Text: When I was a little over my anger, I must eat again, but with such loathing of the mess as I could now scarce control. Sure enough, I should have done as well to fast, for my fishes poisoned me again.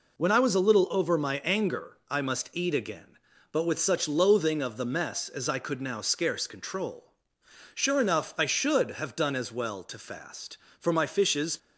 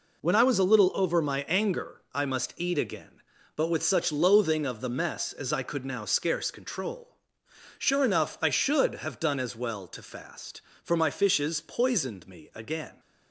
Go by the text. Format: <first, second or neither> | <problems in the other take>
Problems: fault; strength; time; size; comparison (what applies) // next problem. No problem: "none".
second | stops before "poisoned me again"; at 11.5 s